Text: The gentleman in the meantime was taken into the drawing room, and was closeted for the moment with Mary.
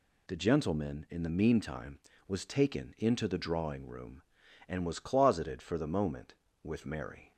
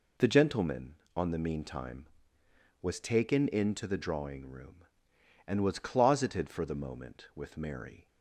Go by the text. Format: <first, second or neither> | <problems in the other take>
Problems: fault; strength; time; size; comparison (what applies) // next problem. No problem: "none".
first | says "on" for "in"; at 1.1 s